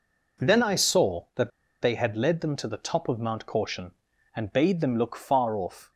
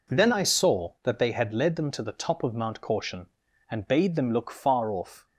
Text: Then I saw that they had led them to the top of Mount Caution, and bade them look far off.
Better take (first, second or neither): second